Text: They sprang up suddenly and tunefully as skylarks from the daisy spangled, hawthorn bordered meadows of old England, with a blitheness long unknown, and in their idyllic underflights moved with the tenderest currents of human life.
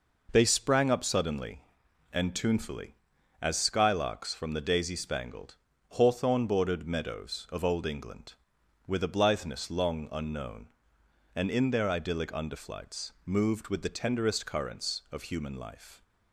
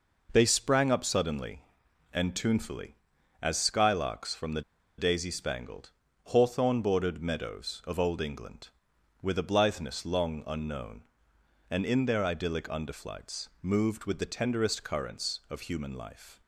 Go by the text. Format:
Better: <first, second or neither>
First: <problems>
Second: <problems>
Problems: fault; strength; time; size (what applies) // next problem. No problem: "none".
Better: first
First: none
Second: pauses between "the" and "daisy"; at 4.6 s; 0.37 s long